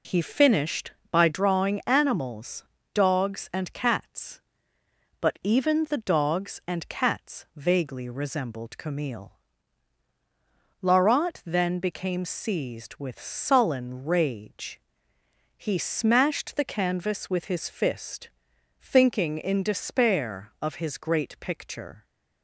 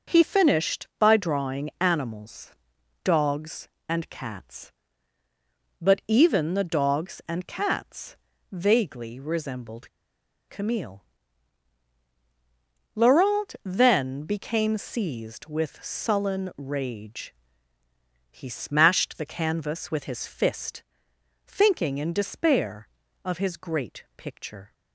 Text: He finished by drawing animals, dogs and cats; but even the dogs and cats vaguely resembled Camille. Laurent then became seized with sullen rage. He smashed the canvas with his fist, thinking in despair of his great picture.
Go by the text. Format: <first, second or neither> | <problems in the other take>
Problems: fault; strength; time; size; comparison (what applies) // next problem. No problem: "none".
first | pauses between "cats" and "vaguely"; slight; at 8.1 s; 0.34 s long // pauses between "resembled" and "Camille"; noticeable; at 9.8 s; 0.59 s long